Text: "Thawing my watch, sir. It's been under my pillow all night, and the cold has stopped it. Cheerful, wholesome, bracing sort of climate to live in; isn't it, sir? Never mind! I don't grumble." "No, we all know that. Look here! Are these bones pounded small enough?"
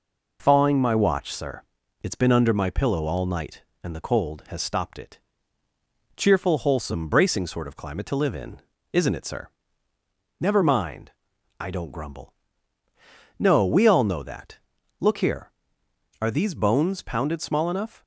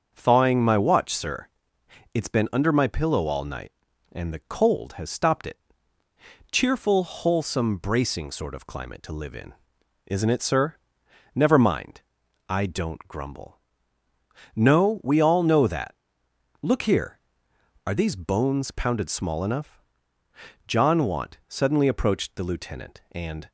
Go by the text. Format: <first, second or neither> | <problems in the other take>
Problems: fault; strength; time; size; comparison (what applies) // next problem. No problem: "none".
first | starts louder than the rest; until 1.1 s; 6.5 dB // goes on to say "John Want suddenly approached the lieutenant and"; strong; from 20.6 s on; 2.8 s long